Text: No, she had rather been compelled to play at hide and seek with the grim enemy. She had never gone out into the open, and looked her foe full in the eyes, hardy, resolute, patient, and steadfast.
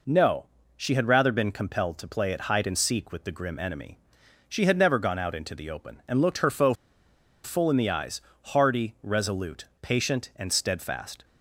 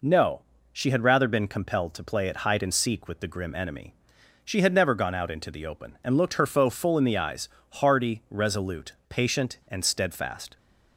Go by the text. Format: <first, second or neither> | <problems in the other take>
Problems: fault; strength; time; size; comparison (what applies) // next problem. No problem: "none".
second | pauses between "foe" and "full"; noticeable; at 6.7 s; 0.69 s long